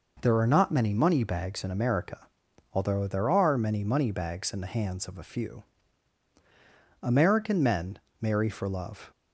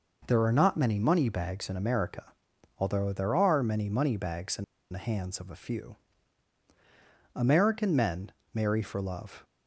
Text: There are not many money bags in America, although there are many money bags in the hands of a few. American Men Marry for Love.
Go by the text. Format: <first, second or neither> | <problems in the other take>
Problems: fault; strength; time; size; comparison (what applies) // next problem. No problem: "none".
first | pauses between "in" and "the"; slight; at 4.6 s; 0.27 s long // pauses between "Men" and "Marry"; slight; at 8.3 s; 0.20 s long; slight in the first